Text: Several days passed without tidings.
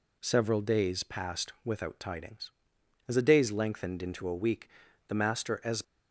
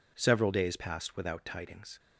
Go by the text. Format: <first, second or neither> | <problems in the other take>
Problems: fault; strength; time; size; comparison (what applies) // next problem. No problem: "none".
second | goes on to say "As the days lengthened into a week the master as"; strong; from 3.0 s on; 2.7 s long